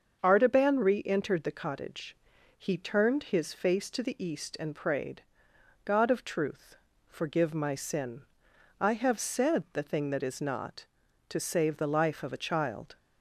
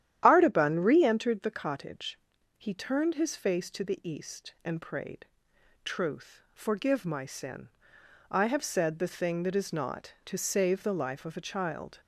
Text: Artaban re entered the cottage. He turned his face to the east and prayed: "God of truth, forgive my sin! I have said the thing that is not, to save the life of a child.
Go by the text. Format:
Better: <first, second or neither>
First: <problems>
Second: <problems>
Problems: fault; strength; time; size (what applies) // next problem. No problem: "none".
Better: first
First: starts louder than the rest; until 1.2 s; 6.5 dB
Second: starts louder than the rest; strong; until 1.2 s; 11 dB // skips "God of"; at 5.5 s